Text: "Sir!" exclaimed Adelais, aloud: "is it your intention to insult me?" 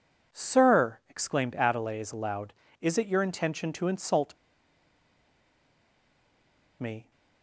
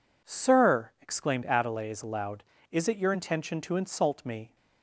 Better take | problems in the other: second | pauses between "insult" and "me"; strong; at 4.3 s; 2.4 s long

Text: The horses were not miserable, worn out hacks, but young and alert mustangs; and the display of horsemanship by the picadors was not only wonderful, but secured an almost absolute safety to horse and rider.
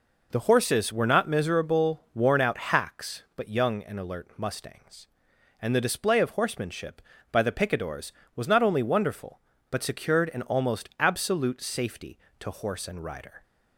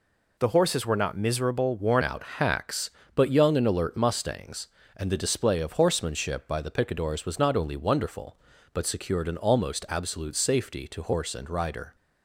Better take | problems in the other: first | changes voice at "out"; from 2.0 s on; 9.9 s long

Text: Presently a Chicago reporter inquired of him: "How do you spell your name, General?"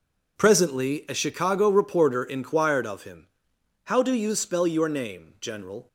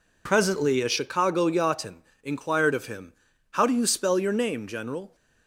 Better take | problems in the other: first | says "yachtin" for "reporter"; at 1.4 s

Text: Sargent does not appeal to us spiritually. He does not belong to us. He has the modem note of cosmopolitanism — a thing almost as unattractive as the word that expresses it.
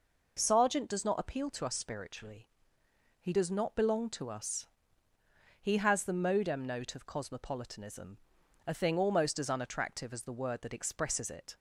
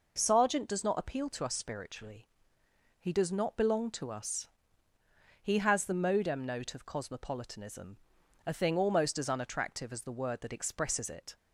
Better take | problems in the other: neither | none

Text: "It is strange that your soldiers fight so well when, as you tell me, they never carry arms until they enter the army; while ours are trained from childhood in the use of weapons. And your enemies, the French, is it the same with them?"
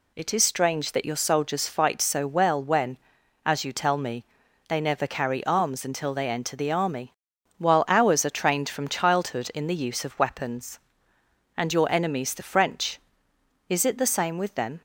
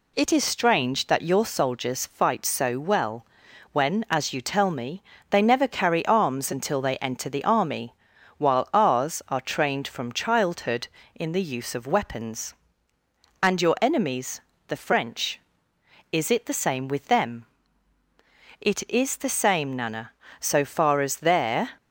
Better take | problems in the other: first | pauses between "well" and "when"; noticeable; at 3.2 s; 0.46 s long // goes on to say "It is the same Nana so far as their"; strong; from 18.6 s on; 3.1 s long

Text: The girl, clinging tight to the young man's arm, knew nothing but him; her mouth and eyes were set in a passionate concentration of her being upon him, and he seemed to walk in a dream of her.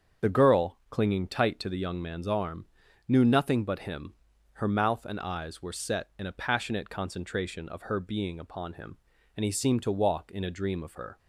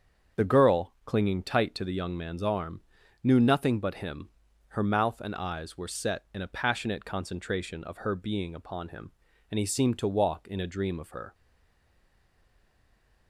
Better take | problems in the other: first | starts louder than the rest; strong; until 1.4 s; 7.5 dB; strong in the first // stays silent after the last word; noticeable; from 11.3 s on; 1.9 s long

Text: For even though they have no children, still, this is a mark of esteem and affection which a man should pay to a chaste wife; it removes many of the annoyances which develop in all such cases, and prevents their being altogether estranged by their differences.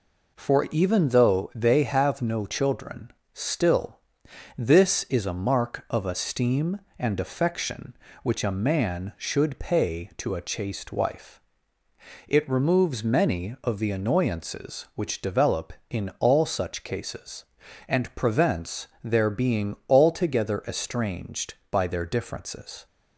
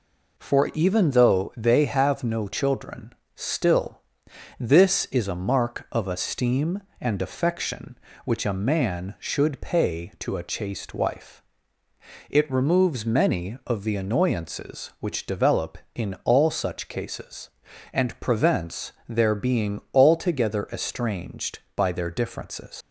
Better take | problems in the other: first | pauses between "prevents" and "their"; slight; at 18.9 s; 0.16 s long; slight in the first // leaves "differences" unfinished; at 22.8 s; 100 ms

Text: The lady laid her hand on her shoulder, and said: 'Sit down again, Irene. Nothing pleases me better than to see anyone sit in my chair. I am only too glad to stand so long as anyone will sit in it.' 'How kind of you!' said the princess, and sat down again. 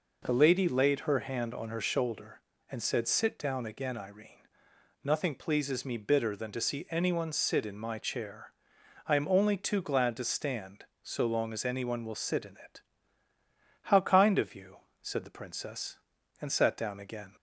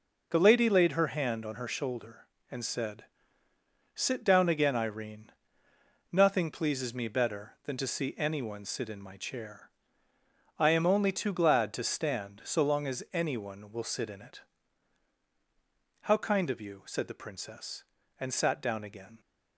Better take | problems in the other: second | says "bitter" for "better"; at 5.9 s

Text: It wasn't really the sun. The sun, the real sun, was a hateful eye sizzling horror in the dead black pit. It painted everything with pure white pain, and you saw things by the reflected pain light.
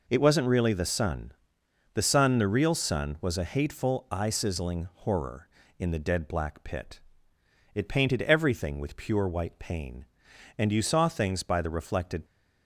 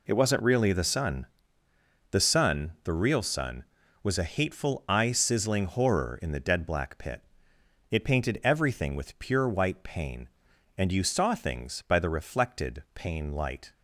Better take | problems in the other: second | stops before "pain light"; at 12.2 s

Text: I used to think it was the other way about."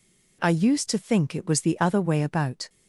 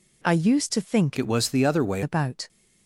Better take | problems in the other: first | changes voice from "it" to "way"; from 1.1 to 2.0 s; 0.9 s long

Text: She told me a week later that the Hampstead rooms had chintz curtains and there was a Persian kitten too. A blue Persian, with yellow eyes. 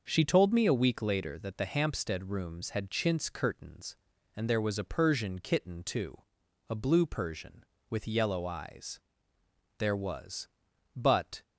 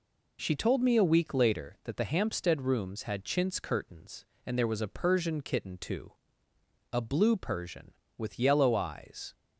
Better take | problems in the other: second | starts louder than the rest; noticeable; until 1.0 s; 6 dB // goes on to say "There was But"; from 9.7 s on; 1.6 s long

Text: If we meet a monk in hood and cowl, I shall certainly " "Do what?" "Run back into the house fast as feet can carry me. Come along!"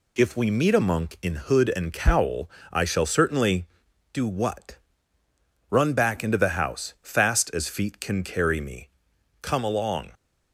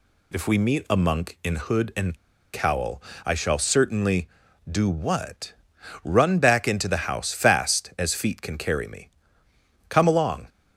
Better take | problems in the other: first | pauses between "and" and "cowl"; at 2.1 s; 0.37 s long

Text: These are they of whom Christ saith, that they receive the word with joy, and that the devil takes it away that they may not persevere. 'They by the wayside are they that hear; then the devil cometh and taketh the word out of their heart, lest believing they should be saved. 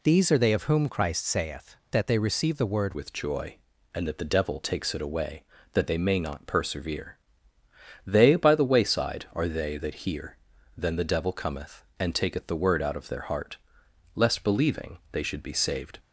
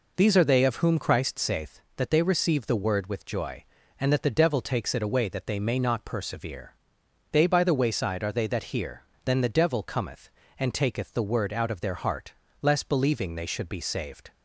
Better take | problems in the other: second | changes voice at "with"; from 2.9 s on; 13.0 s long

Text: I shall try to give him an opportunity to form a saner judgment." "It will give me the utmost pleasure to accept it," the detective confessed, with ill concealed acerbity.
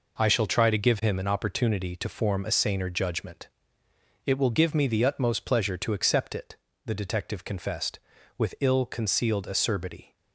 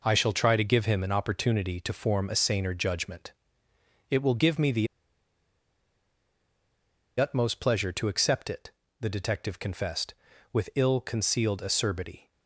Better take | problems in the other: first | pauses between "the" and "utmost"; strong; at 4.8 s; 2.3 s long

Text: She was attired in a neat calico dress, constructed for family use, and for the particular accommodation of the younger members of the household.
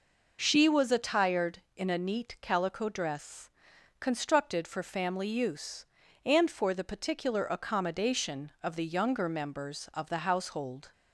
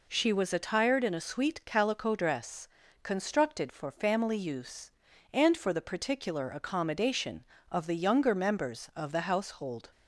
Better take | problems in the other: first | says "sweet" for "neat"; at 1.2 s

